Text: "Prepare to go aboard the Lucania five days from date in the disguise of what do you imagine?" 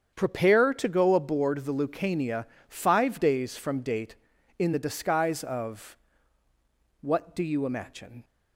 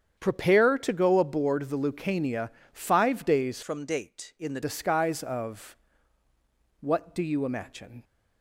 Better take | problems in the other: first | starts louder than the rest; strong; until 1.2 s; 8.5 dB; strong in the first // pauses between "Lucania" and "five"; slight; at 2.4 s; 0.24 s long; slight in the first // changes voice from "from" to "the"; from 3.6 to 4.5 s; 0.9 s long // pauses between "of" and "what"; at 5.7 s; 1.0 s long; also in the first

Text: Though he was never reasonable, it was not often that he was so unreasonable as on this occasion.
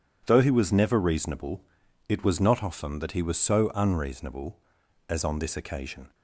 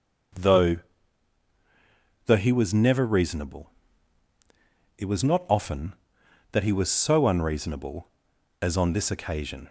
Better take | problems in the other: first | says "Though" twice; at 2.2 s

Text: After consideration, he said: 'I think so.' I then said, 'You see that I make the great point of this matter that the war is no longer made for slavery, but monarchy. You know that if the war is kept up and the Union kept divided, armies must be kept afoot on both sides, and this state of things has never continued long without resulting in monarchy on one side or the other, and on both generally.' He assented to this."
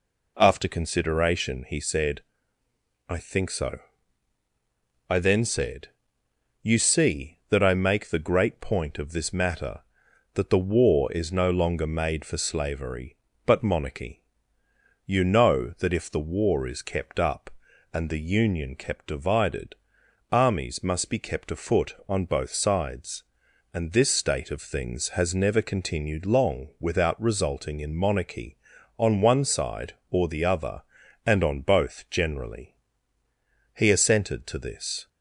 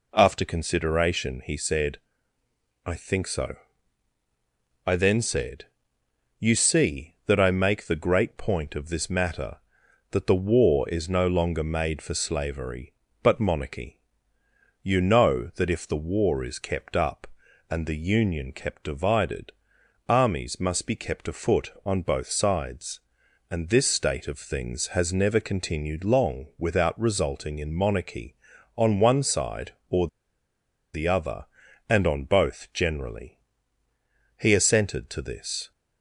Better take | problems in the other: first | pauses between "or" and "the"; noticeable; at 30.0 s; 0.86 s long

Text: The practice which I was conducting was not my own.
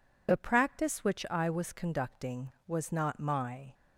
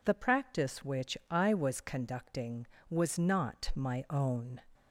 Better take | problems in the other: second | stops before "own"; at 3.7 s

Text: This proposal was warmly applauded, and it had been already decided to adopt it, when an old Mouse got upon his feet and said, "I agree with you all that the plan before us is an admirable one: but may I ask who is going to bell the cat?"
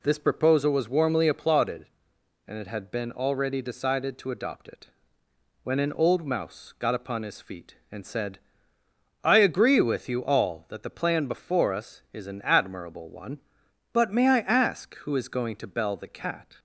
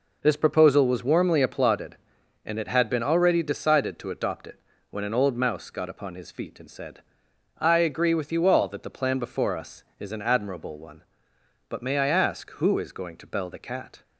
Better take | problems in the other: neither | none

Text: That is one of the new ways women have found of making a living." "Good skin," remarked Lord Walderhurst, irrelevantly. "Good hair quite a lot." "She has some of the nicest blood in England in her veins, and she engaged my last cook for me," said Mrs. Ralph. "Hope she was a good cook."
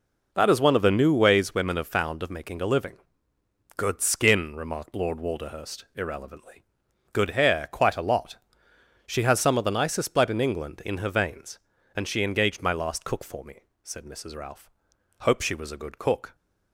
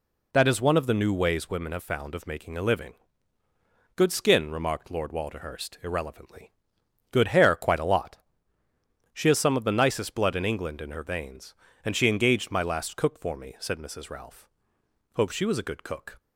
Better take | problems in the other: neither | none

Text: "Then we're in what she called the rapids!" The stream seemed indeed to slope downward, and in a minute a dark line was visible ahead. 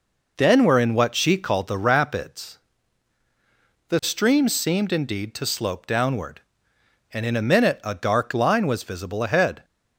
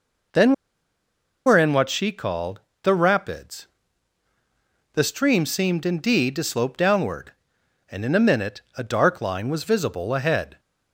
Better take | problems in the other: first | pauses between "Then" and "we're"; noticeable; at 0.5 s; 0.94 s long // pauses between "called" and "the"; slight; at 2.6 s; 0.22 s long // pauses between "minute" and "a"; slight; at 8.6 s; 0.16 s long

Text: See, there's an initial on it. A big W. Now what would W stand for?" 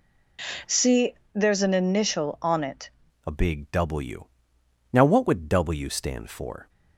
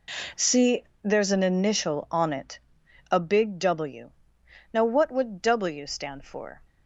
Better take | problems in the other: second | changes voice at "A"; from 3.2 s on; 3.4 s long

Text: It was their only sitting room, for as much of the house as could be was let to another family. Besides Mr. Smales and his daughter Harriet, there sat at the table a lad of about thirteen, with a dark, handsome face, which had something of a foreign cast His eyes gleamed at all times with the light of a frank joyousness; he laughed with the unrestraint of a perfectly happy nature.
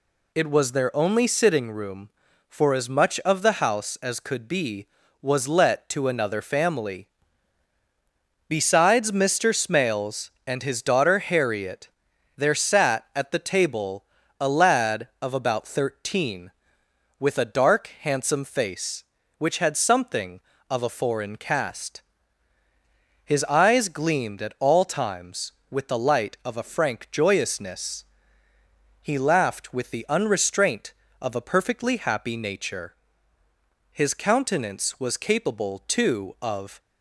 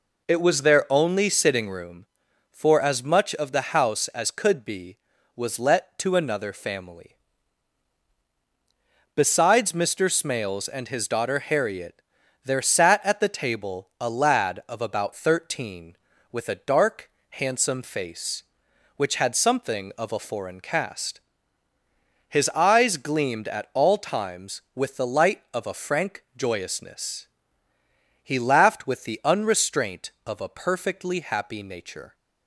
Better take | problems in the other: second | pauses between "table" and "a"; slight; at 14.0 s; 0.36 s long // pauses between "cast" and "His"; at 22.0 s; 1.2 s long; also in the second // goes on to say "His countenance was capable too of"; strong; from 33.9 s on; 2.8 s long

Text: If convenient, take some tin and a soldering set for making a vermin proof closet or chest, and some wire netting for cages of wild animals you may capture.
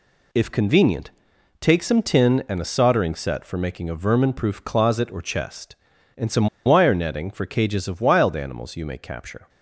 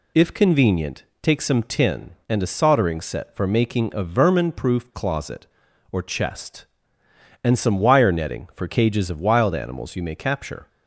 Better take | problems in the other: second | pauses between "some" and "wire"; slight; at 6.4 s; 0.18 s long

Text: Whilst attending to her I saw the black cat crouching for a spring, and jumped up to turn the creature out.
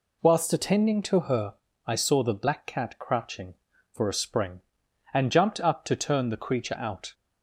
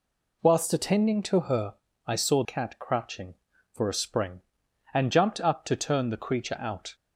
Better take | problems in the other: first | pauses between "her" and "I"; slight; at 1.7 s; 0.32 s long; slight in the first // skips "the black"; at 2.4 s

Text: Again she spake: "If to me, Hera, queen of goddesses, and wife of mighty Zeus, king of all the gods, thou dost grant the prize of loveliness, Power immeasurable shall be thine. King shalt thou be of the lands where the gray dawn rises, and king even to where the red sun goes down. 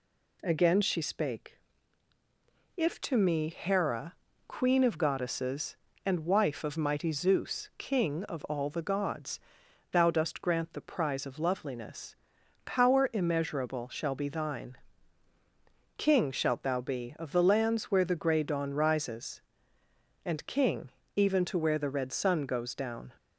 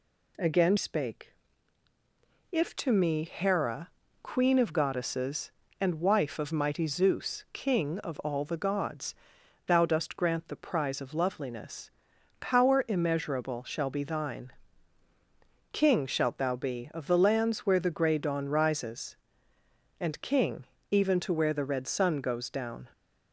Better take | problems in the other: first | skips "she"; at 0.7 s // pauses between "king" and "even"; slight; at 20.6 s; 0.26 s long; slight in the first

